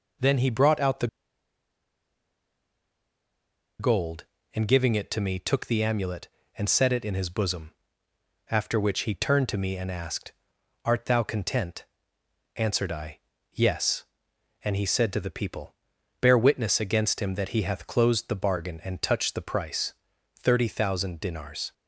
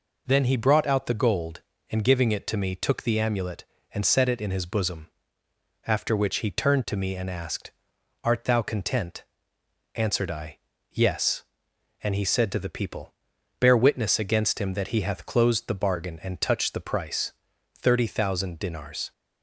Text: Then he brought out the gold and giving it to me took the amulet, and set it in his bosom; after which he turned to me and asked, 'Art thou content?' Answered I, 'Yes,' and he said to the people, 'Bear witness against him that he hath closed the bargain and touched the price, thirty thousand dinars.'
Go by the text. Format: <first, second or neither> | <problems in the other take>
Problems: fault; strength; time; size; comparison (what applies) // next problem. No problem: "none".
second | pauses between "the" and "gold"; strong; at 1.0 s; 2.7 s long